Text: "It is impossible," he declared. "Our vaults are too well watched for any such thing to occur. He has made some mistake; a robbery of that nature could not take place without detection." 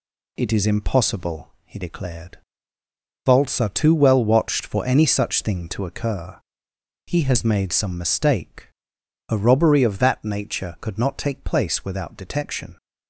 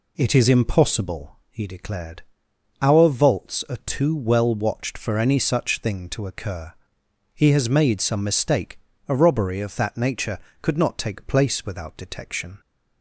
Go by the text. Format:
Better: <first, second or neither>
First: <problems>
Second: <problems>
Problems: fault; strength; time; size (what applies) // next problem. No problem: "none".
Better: second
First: skips "Our"; at 2.8 s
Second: none